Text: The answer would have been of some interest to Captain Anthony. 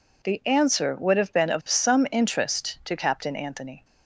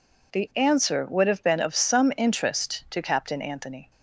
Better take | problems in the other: neither | none

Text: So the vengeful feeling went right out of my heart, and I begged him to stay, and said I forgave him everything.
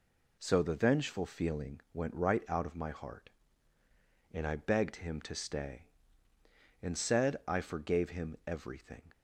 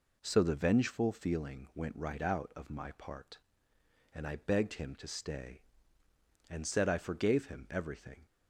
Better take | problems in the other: first | says "part" for "heart"; at 2.9 s

